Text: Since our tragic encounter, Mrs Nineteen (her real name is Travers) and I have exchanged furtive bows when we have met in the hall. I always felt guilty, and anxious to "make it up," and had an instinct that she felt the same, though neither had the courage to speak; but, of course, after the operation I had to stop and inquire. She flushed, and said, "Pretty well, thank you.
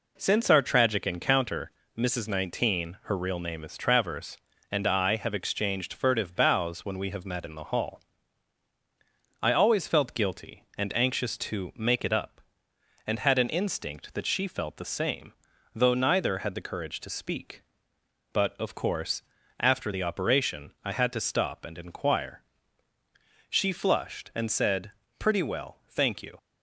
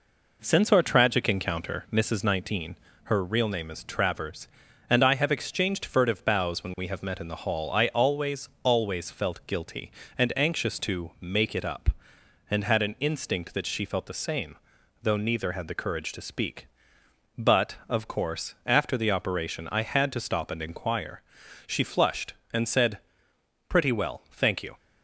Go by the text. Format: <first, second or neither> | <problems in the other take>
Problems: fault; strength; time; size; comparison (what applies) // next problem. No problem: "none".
first | says "always" twice; at 8.6 s